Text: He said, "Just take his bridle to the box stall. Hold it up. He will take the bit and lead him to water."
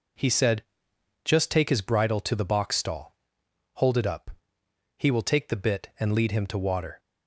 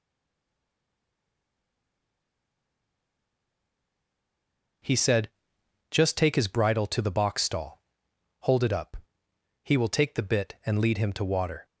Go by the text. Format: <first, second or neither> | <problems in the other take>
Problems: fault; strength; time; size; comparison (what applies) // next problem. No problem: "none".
first | stays silent before the first word; strong; until 4.8 s; 4.8 s long